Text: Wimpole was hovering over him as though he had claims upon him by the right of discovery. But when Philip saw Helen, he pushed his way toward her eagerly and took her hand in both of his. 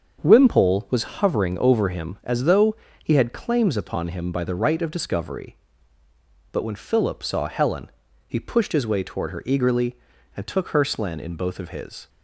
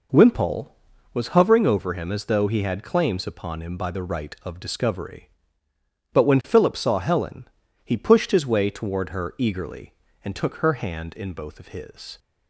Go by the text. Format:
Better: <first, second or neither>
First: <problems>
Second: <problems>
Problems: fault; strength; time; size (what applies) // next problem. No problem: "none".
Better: second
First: starts louder than the rest; until 1.2 s; 7 dB // pauses between "though" and "he"; slight; at 2.7 s; 0.28 s long // says "slen" for "hand"; at 10.8 s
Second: none